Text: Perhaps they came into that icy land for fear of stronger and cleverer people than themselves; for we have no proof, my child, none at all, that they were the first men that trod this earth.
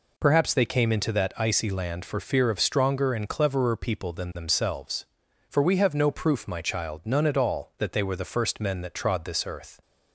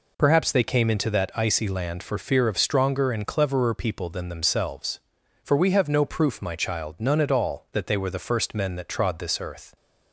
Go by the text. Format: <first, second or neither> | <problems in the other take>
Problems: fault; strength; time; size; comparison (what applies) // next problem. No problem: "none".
neither | none